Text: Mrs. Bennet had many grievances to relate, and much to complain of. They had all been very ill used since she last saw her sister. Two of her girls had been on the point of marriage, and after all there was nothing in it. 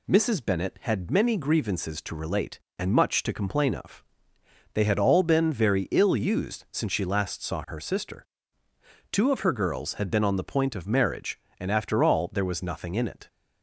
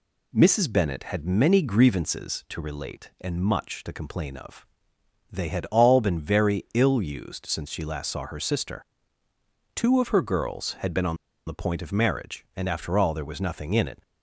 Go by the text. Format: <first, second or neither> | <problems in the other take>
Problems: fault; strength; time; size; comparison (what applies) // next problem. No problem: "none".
first | pauses between "on" and "the"; slight; at 11.1 s; 0.31 s long